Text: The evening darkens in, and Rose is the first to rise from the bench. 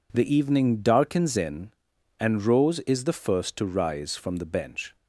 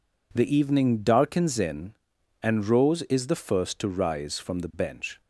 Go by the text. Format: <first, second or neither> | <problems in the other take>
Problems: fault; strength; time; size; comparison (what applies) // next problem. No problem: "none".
neither | none